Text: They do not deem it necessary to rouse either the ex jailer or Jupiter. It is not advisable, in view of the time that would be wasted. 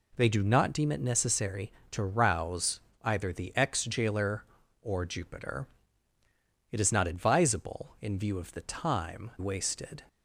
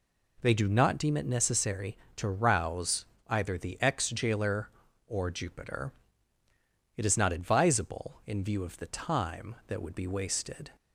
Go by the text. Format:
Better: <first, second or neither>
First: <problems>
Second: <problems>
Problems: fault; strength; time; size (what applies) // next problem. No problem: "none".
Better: second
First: pauses between "rouse" and "either"; slight; at 2.7 s; 0.22 s long // skips "that would be"; at 9.3 s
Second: pauses between "rouse" and "either"; slight; at 3.0 s; 0.22 s long